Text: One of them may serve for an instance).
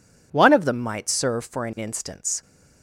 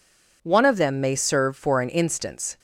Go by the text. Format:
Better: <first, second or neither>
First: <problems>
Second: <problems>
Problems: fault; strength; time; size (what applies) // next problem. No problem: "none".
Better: second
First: says "might" for "may"; at 0.7 s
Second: none